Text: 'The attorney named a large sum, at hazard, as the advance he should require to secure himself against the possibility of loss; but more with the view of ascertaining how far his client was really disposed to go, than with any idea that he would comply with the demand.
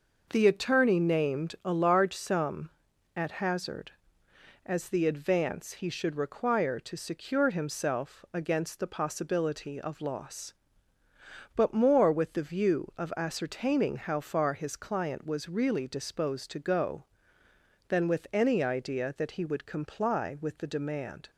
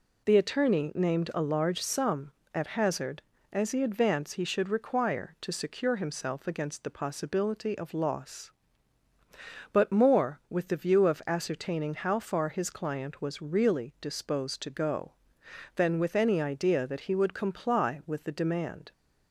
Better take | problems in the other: neither | none

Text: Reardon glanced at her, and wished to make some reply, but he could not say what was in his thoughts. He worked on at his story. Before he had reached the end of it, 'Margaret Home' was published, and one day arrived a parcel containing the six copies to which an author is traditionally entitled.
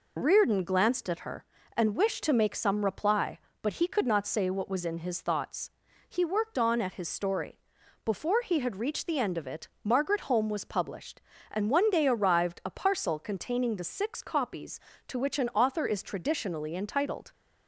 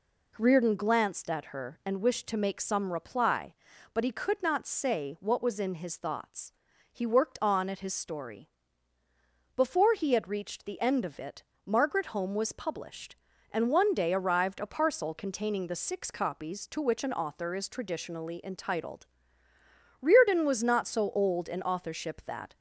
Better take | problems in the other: first | goes on to say "Reardon was not so old in authorship that"; strong; from 20.0 s on; 2.5 s long

